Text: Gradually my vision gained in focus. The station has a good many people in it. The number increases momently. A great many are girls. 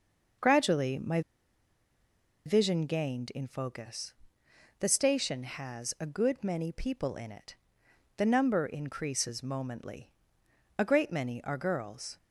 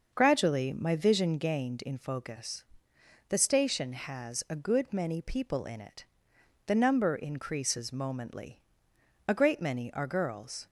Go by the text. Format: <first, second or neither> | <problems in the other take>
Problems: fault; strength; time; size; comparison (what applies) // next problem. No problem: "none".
second | starts louder than the rest; until 2.6 s; 6.5 dB; also in the second // pauses between "my" and "vision"; strong; at 1.2 s; 1.2 s long